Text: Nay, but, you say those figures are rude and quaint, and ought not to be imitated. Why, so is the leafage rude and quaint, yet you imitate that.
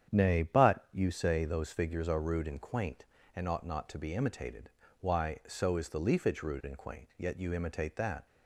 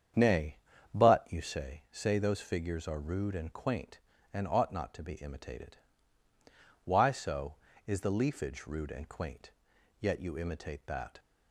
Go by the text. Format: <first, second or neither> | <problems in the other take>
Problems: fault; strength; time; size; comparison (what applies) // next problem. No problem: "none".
first | starts louder than the rest; strong; until 1.5 s; 8 dB; strong in the first // says "say" twice; at 1.9 s